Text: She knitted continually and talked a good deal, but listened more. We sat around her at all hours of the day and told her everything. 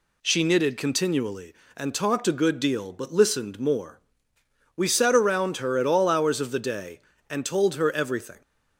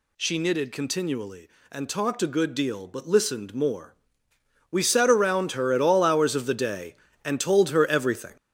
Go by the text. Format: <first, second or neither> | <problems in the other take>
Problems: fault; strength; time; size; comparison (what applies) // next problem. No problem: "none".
first | gets louder; strong; throughout; 7.5 dB